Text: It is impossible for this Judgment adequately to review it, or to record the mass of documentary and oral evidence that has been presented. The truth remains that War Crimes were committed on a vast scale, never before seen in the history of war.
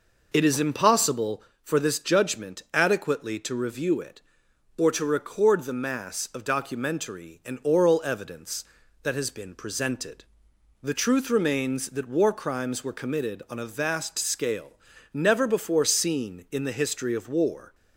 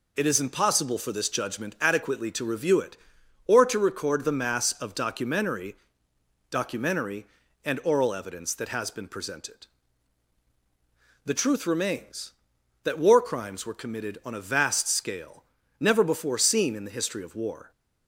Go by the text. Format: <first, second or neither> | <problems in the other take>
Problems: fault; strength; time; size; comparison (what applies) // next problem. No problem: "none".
first | says "documentary" twice; at 6.5 s